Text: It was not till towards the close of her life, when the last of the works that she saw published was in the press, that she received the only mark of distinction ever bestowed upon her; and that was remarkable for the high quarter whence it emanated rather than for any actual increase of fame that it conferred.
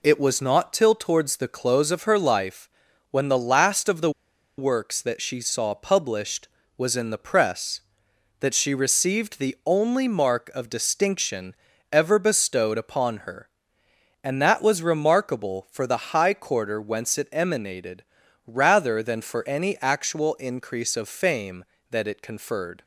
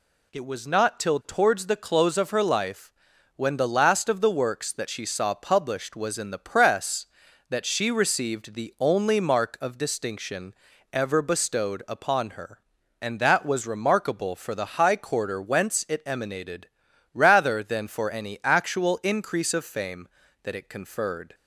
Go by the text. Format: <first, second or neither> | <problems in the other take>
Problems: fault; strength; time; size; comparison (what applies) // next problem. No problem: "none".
second | pauses between "the" and "works"; noticeable; at 4.0 s; 0.48 s long // pauses between "distinction" and "ever"; at 11.5 s; 0.38 s long; also in the second // pauses between "emanated" and "rather"; at 18.0 s; 0.42 s long; also in the second